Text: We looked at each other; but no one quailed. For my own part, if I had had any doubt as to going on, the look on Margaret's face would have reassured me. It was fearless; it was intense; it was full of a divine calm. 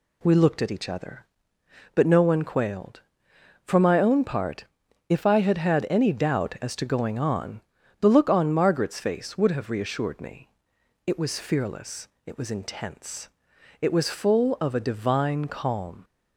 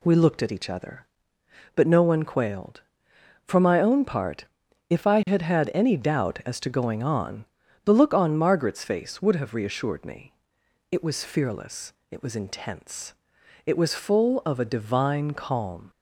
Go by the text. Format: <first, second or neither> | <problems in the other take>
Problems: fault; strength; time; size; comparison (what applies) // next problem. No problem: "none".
neither | none